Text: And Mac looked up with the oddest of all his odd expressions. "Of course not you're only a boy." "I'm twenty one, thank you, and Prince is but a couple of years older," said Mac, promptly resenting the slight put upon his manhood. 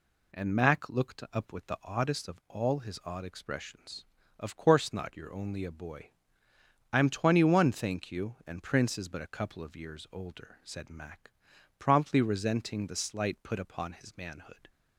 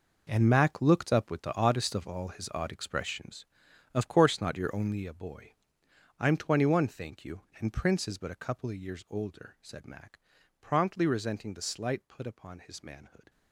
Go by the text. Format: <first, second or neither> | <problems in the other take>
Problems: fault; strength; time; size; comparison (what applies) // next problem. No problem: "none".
first | gets quieter; strong; throughout; 13.5 dB